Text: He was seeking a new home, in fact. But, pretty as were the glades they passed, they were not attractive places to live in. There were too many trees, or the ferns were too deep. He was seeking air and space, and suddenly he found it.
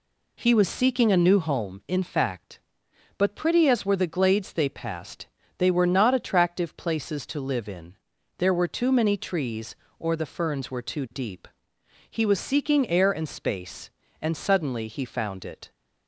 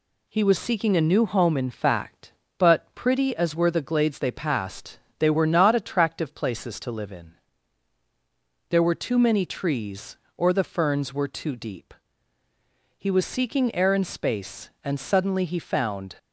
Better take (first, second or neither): first